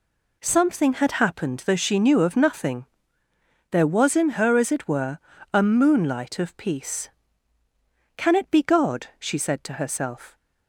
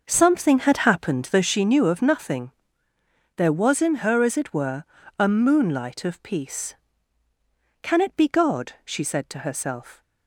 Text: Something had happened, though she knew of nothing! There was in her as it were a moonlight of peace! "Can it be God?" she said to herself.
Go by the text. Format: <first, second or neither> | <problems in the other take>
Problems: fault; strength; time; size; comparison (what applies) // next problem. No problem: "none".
first | starts louder than the rest; noticeable; until 1.7 s; 6 dB // pauses between "were" and "a"; slight; at 4.8 s; 0.34 s long; slight in the first